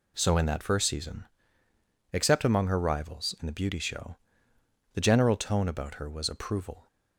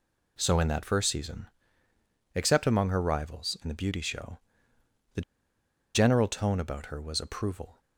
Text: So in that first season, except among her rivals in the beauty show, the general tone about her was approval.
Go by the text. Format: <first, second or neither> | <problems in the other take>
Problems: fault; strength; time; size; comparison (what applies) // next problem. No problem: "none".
first | pauses between "the" and "general"; noticeable; at 5.2 s; 0.73 s long